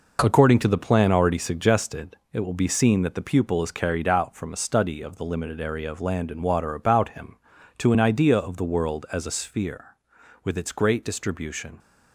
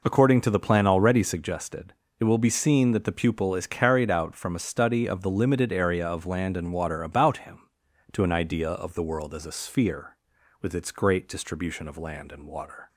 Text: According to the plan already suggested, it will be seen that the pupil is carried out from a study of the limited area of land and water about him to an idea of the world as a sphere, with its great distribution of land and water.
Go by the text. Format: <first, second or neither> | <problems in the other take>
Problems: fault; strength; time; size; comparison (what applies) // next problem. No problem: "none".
second | stops before "of land and water"; at 11.7 s